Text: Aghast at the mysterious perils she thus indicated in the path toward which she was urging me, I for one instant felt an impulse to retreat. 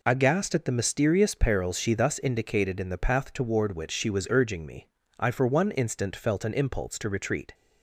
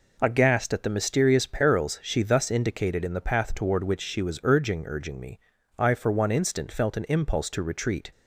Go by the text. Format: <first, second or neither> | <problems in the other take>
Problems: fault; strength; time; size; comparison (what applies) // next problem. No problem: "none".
first | says "urging" twice; at 4.8 s